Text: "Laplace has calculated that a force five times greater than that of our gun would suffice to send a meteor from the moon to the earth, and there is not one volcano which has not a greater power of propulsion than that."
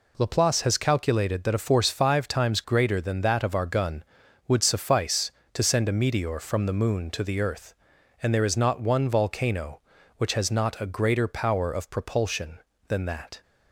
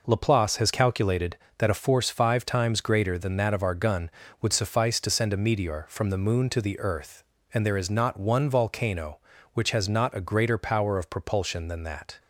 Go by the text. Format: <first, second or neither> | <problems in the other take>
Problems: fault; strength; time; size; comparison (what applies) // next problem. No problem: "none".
neither | none